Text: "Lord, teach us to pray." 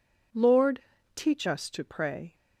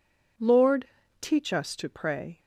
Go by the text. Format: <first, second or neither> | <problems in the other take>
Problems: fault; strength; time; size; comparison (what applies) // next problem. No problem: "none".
neither | none